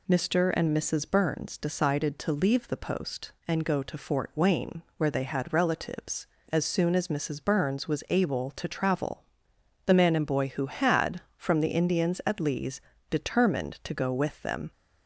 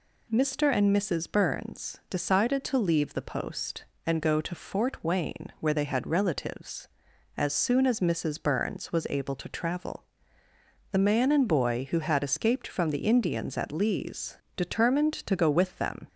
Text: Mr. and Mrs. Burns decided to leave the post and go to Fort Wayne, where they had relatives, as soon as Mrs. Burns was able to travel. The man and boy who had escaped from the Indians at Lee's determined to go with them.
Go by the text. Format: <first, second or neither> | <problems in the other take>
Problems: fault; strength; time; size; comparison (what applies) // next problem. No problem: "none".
second | skips "escaped"; at 11.2 s // pauses between "Lee's" and "determined"; slight; at 12.8 s; 0.30 s long; slight in the second